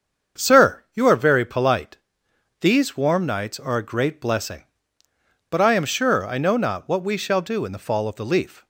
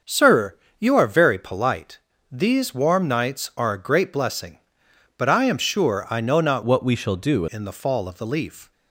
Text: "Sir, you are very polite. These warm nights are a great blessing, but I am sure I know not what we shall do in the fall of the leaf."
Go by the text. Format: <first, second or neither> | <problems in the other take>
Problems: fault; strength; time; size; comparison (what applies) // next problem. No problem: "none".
first | starts louder than the rest; until 1.2 s; 6.5 dB; strong in the first // changes voice from "what" to "do"; from 6.6 to 7.4 s; 0.8 s long